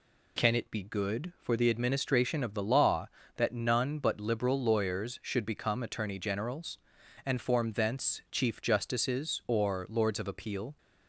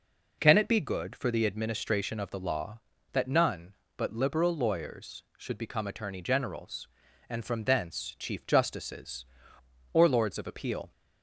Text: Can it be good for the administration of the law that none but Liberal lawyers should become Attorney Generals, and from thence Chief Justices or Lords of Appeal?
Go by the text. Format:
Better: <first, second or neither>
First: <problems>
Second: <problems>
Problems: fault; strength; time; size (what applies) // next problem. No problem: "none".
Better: second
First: says "form" for "from"; at 7.4 s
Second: none